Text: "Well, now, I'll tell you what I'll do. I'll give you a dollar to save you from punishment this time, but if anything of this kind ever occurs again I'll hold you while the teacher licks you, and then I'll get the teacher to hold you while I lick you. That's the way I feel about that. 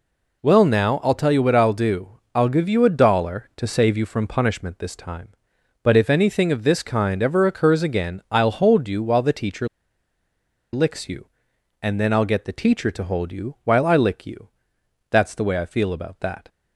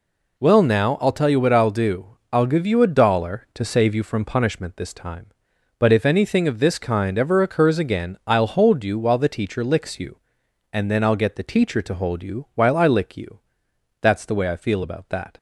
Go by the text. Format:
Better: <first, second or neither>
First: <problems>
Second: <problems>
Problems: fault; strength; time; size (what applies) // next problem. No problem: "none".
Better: second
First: pauses between "teacher" and "licks"; at 9.6 s; 1.0 s long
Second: none